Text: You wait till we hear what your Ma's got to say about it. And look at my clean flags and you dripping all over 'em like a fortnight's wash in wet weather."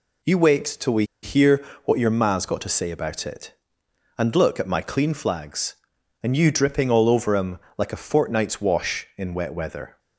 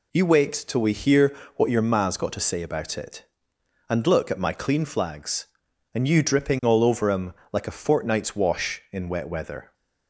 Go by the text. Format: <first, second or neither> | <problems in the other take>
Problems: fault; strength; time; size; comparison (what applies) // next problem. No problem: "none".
second | pauses between "we" and "hear"; slight; at 1.0 s; 0.18 s long // pauses between "hear" and "what"; slight; at 1.6 s; 0.20 s long; slight in the second // pauses between "em" and "like"; slight; at 7.5 s; 0.18 s long; slight in the second